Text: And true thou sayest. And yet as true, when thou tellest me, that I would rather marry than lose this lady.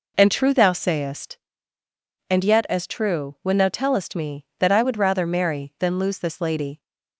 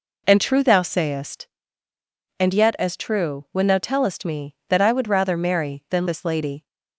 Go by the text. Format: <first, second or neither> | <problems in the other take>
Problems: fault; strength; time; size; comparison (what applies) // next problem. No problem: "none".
first | skips "lose"; at 6.0 s